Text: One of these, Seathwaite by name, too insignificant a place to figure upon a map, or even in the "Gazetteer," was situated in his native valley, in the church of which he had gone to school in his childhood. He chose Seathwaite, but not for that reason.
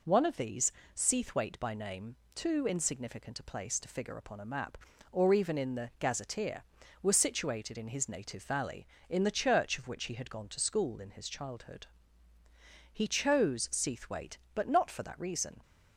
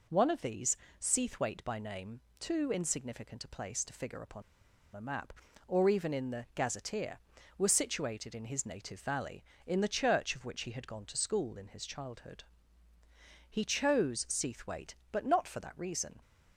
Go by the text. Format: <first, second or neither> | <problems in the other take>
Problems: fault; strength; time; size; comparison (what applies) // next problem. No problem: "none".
first | pauses between "upon" and "a"; noticeable; at 4.4 s; 0.52 s long